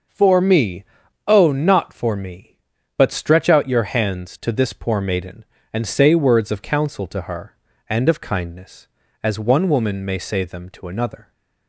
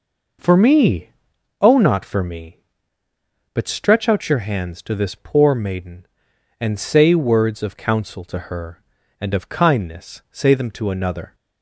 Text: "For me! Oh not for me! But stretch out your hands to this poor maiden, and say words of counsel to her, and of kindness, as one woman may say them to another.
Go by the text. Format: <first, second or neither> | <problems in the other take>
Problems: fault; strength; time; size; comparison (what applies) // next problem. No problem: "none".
first | skips "as one woman may"; at 10.2 s